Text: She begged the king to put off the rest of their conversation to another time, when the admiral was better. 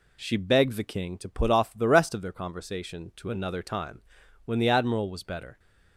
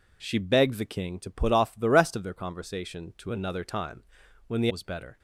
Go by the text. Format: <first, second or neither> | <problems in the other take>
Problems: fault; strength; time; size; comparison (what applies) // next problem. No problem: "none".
first | skips "admiral"; at 4.7 s